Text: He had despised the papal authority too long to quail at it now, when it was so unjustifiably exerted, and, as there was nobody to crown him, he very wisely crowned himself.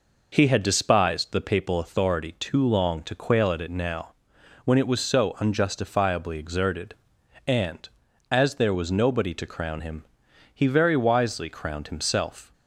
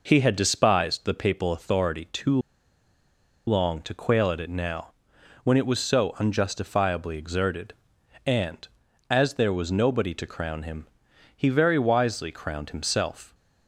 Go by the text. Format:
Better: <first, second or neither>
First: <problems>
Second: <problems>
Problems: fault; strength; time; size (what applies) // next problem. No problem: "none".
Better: first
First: none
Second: pauses between "too" and "long"; at 2.3 s; 1.0 s long